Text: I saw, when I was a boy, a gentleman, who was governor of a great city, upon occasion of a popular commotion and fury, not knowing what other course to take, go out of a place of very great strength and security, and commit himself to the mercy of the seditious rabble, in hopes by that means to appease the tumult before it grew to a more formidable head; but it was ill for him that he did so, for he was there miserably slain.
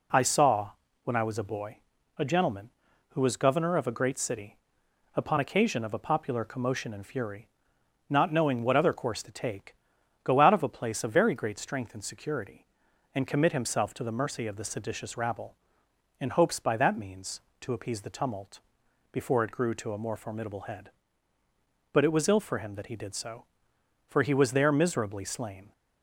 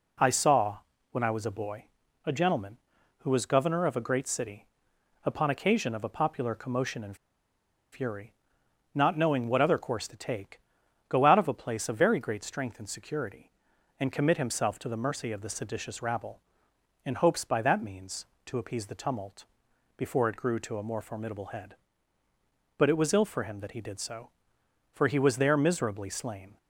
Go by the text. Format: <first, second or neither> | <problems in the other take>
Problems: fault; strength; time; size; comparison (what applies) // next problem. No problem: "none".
first | pauses between "and" and "fury"; noticeable; at 7.1 s; 0.77 s long // pauses between "tumult" and "before"; noticeable; at 19.4 s; 0.52 s long; noticeable in the first